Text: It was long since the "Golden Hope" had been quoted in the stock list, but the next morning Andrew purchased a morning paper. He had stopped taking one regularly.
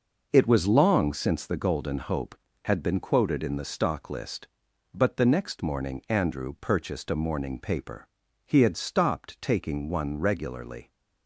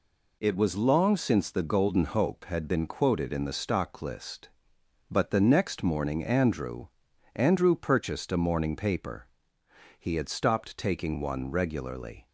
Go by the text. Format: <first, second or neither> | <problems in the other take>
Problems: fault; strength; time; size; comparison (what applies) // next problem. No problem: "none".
first | says "Andrew" twice; at 7.3 s